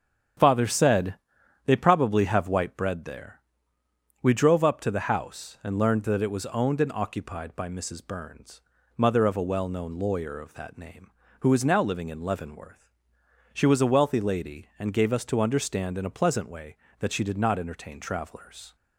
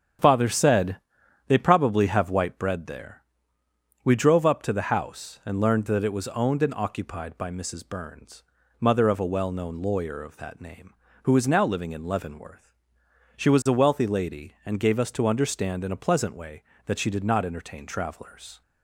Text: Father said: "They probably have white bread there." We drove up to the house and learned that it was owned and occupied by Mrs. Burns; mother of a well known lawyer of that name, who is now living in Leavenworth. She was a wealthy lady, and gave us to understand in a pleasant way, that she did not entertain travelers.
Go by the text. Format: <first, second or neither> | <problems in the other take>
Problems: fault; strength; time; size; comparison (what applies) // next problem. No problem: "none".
neither | starts louder than the rest; strong; the same in both